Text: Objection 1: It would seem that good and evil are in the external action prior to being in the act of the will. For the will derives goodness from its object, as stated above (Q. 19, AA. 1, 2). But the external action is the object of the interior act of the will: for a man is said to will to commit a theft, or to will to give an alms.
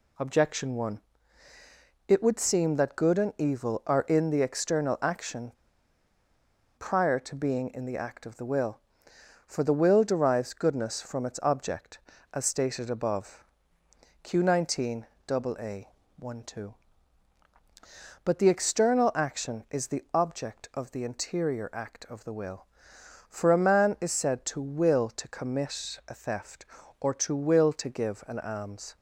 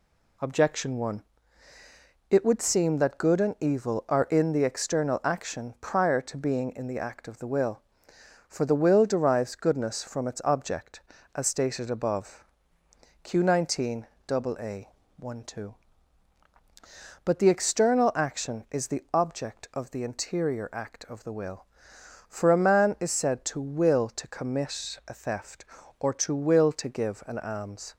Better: second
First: pauses between "action" and "prior"; strong; at 5.5 s; 1.2 s long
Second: none

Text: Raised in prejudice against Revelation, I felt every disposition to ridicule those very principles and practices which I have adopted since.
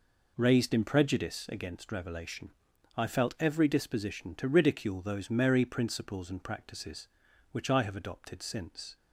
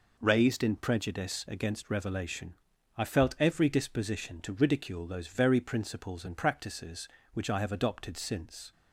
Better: second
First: says "merry" for "very"; at 5.2 s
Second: none

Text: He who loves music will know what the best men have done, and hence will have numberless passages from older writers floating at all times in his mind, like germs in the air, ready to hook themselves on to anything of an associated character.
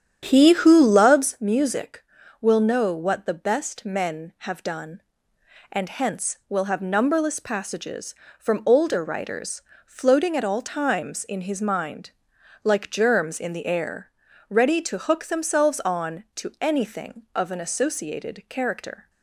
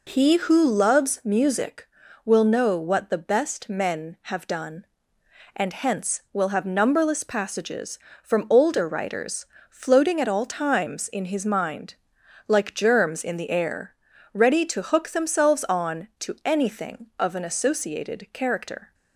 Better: second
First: starts louder than the rest; strong; until 1.4 s; 9.5 dB // pauses between "writers" and "floating"; slight; at 9.5 s; 0.24 s long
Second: pauses between "writers" and "floating"; slight; at 9.4 s; 0.24 s long

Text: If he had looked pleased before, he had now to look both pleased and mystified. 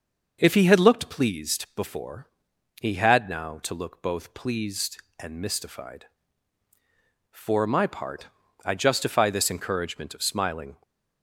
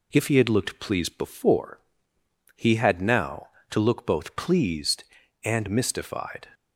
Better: second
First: starts louder than the rest; until 1.4 s; 6 dB // goes on to say "For my part I justify this encouragement of smiling"; strong; from 7.2 s on; 3.5 s long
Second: none

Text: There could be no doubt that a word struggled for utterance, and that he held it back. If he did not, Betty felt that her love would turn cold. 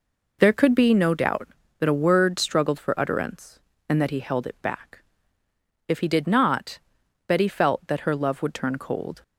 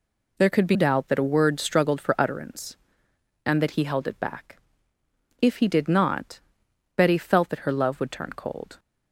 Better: first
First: none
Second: skips "no"; at 0.7 s

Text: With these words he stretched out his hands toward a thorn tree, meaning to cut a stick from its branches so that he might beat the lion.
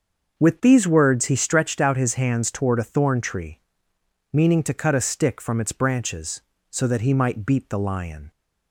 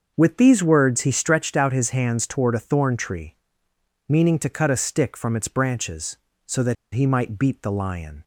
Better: first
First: starts louder than the rest; until 1.4 s; 6.5 dB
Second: starts louder than the rest; until 1.1 s; 6.5 dB // pauses between "that" and "he"; slight; at 6.7 s; 0.20 s long

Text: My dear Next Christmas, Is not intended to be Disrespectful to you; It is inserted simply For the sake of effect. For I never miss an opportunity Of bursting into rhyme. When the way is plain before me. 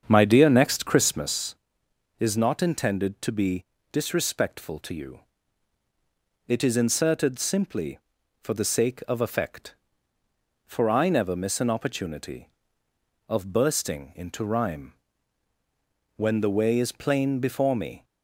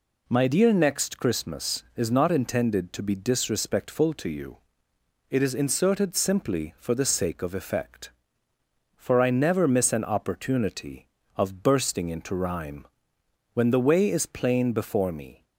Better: second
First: starts louder than the rest; strong; until 1.3 s; 7.5 dB // pauses between "be" and "Disrespectful"; slight; at 3.6 s; 0.28 s long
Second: none

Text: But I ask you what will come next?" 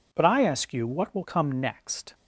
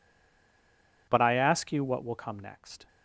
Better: first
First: none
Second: stays silent before the first word; until 1.0 s; 1.0 s long

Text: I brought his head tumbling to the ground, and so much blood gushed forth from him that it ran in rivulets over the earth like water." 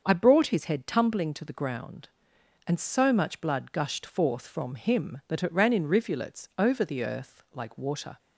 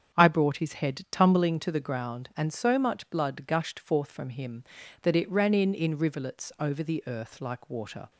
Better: first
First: starts louder than the rest; until 1.0 s; 6.5 dB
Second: starts louder than the rest; strong; until 1.1 s; 7.5 dB // says "in" twice; at 5.7 s

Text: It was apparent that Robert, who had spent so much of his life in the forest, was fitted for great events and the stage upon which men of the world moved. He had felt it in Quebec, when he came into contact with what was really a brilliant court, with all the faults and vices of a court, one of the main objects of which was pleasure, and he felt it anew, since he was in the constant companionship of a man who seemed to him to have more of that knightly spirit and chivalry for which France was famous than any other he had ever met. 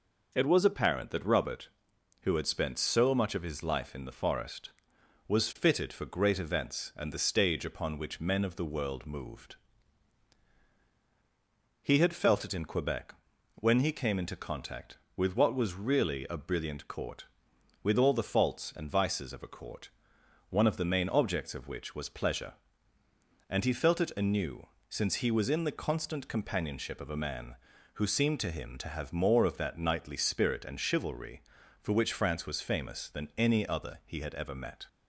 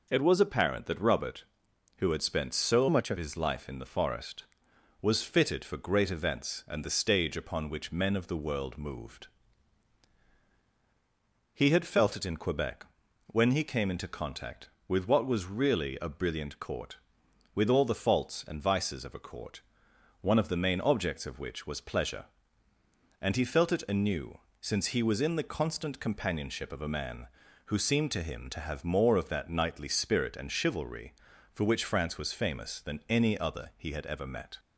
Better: first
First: none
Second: changes voice from "much" to "of"; from 2.8 to 3.1 s; 0.3 s long

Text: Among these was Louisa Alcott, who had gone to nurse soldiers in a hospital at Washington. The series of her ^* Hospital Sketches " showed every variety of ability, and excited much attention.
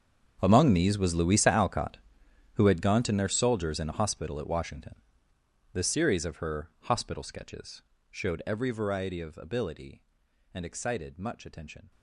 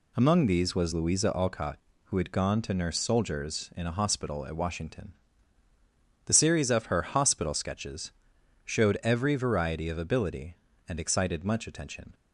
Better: second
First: gets quieter; strong; throughout; 19.5 dB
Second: none

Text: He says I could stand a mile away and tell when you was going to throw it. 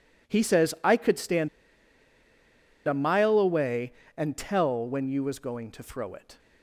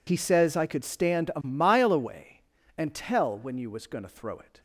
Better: second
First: pauses between "stand" and "a"; strong; at 1.4 s; 1.3 s long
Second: none

